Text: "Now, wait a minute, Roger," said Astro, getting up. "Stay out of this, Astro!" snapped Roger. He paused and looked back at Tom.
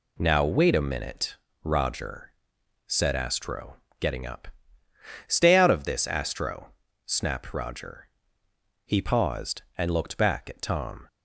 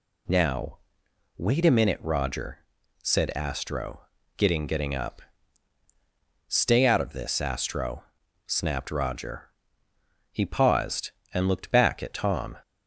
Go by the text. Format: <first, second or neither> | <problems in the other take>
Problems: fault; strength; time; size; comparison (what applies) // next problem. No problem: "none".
first | says "getting" twice; at 4.6 s